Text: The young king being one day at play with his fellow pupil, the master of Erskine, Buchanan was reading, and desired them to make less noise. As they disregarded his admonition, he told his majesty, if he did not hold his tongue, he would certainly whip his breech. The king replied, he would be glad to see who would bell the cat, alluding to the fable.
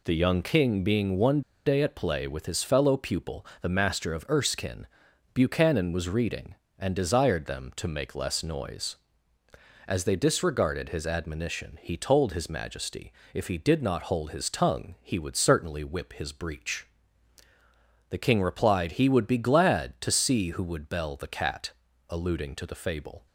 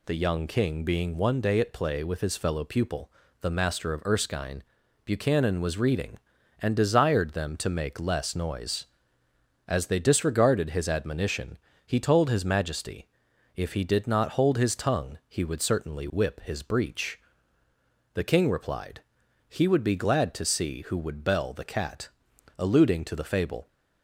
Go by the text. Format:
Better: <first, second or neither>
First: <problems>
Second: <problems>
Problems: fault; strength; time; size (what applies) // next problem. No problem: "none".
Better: second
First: pauses between "one" and "day"; slight; at 1.4 s; 0.25 s long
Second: none